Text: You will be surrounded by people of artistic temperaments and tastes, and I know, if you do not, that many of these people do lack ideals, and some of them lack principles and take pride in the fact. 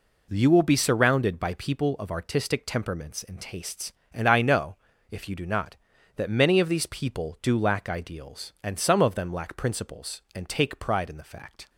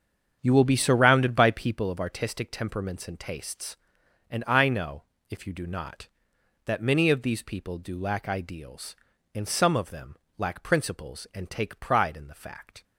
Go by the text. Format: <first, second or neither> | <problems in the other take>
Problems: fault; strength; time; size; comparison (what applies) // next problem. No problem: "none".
first | starts louder than the rest; strong; until 1.9 s; 7.5 dB // pauses between "them" and "lack"; slight; at 10.1 s; 0.22 s long